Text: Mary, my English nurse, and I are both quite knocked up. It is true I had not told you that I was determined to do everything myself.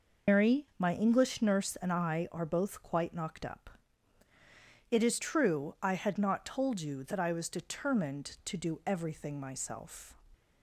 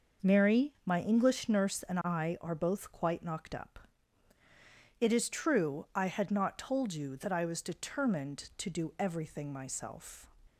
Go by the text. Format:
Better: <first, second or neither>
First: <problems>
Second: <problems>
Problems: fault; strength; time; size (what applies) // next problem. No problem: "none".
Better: second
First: loses the start of "Mary"; at 0.2 s; 150 ms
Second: none